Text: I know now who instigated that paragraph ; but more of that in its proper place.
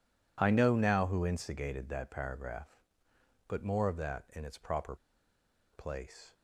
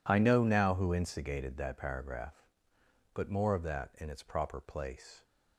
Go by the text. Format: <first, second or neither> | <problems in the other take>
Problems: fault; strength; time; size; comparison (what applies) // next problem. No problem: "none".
second | pauses between "proper" and "place"; noticeable; at 4.9 s; 0.78 s long